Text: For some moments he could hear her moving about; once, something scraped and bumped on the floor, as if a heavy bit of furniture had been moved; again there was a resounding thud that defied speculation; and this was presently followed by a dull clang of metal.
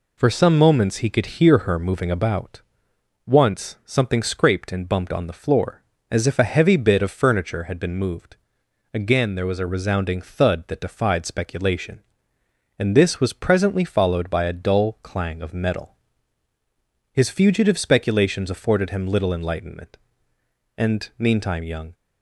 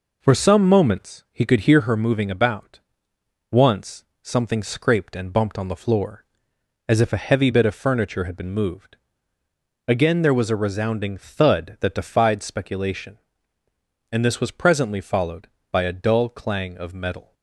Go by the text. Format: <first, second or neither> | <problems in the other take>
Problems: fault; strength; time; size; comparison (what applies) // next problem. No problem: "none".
second | goes on to say "His fugitive speculations afforded him little enlightenment and meantime young"; strong; from 17.1 s on; 4.8 s long